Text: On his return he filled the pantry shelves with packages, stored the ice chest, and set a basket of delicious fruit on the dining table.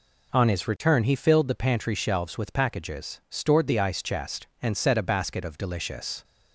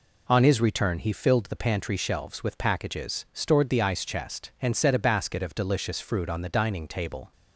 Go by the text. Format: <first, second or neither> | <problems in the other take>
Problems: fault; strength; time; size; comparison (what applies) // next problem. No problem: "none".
second | stops before "fruit on the dining table"; at 6.2 s